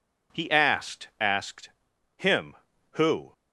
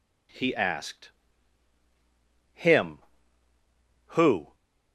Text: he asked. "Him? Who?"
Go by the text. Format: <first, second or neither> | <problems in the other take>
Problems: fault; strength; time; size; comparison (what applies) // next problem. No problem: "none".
second | says "asked" twice; at 1.1 s